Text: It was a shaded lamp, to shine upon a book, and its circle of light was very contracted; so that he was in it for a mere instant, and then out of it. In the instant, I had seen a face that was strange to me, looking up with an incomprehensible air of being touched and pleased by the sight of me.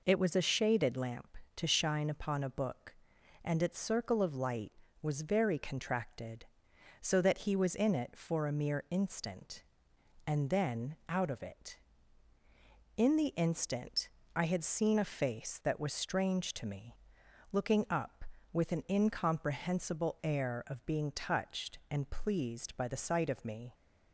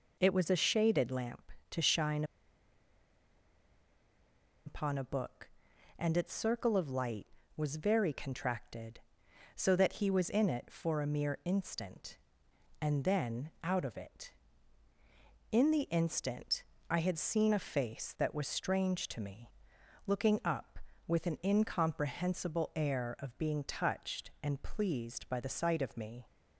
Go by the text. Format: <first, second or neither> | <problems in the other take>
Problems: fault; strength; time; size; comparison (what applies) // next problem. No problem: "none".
first | pauses between "shine" and "upon"; strong; at 2.2 s; 2.4 s long